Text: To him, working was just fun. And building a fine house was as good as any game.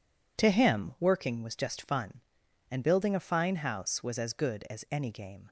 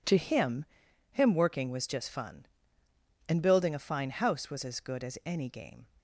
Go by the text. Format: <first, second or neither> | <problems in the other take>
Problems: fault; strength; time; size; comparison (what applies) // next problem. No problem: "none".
first | says "him" twice; at 1.1 s